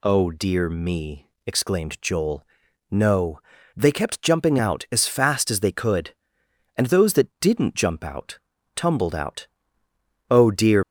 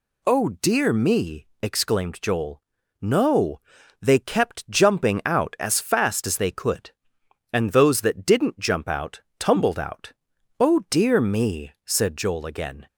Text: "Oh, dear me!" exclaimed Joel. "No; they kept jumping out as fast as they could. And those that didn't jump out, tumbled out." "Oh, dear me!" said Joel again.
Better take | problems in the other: second | stops before "me said Joel again"; at 10.8 s

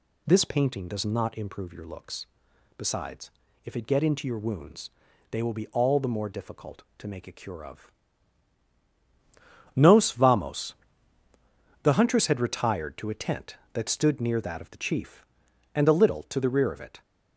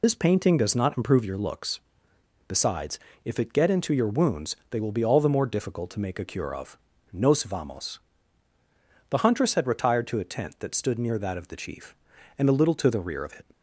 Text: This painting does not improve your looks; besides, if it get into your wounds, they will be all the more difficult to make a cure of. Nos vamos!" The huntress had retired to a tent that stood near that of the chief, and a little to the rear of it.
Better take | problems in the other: first | loses the start of "This"; at 0.0 s; 50 ms

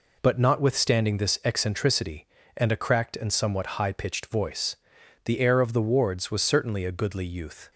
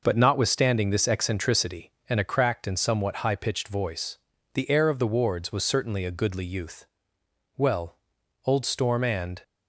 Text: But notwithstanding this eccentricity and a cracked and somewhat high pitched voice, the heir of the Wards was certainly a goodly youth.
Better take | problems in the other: first | goes on to say "Well old Storm and"; strong; from 7.5 s on; 1.8 s long

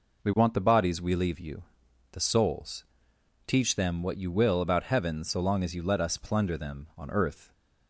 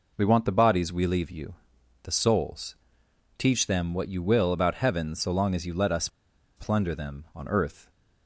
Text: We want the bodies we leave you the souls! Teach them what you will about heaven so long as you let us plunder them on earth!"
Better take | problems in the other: first | pauses between "you" and "the"; noticeable; at 1.5 s; 0.50 s long; noticeable in the first // pauses between "us" and "plunder"; noticeable; at 6.0 s; 0.49 s long

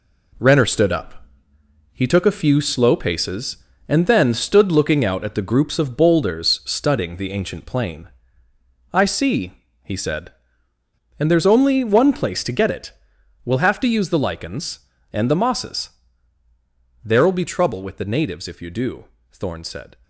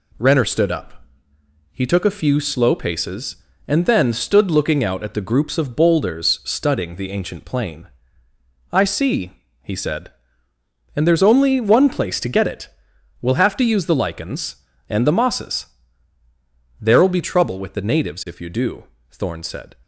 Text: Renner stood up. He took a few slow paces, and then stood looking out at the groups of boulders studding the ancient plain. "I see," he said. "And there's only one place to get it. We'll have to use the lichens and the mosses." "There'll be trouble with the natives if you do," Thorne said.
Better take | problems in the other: second | gets quieter; throughout; 6.5 dB

